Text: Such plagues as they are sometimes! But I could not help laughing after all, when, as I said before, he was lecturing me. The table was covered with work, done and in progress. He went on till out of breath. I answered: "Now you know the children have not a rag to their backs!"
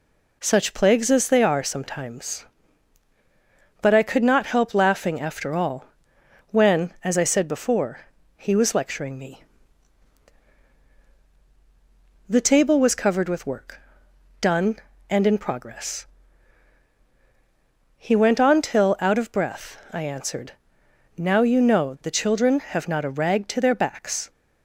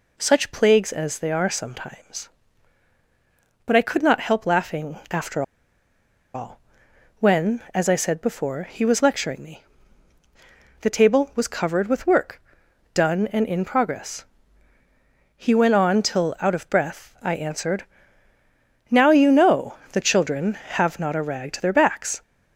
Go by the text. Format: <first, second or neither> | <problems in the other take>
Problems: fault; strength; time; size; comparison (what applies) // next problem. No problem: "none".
first | pauses between "after" and "all"; noticeable; at 5.4 s; 0.91 s long // pauses between "know" and "the"; slight; at 19.7 s; 0.16 s long